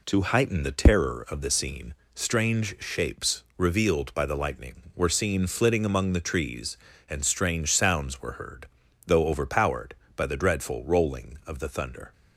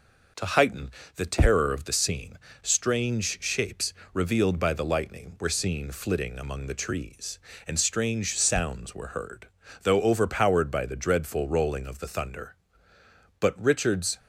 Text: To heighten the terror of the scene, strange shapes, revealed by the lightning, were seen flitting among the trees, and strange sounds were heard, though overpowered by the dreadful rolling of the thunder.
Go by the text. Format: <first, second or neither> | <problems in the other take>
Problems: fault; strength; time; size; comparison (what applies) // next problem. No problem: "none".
first | pauses between "heighten" and "the"; slight; at 0.8 s; 0.24 s long // goes on to say "But Richard's"; noticeable; from 13.3 s on; 0.78 s long